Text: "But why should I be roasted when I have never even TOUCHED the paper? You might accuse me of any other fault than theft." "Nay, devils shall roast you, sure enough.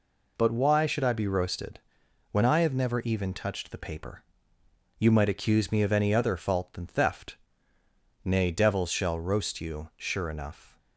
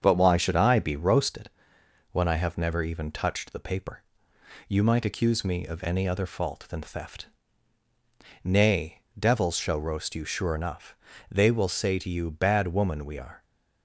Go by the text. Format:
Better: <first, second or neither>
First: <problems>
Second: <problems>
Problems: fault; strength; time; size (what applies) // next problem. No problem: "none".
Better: first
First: pauses between "roasted" and "when"; noticeable; at 1.7 s; 0.52 s long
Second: starts louder than the rest; strong; until 1.0 s; 7 dB // pauses between "roasted" and "when"; noticeable; at 1.4 s; 0.62 s long // goes on to say "They will say to you Bad woman we are"; strong; from 11.3 s on; 2.1 s long